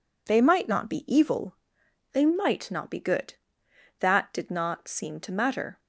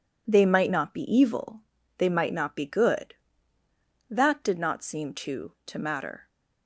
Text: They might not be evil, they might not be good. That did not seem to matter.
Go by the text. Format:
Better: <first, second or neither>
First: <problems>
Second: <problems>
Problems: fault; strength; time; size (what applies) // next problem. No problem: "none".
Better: first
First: none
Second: says "to" twice; at 5.6 s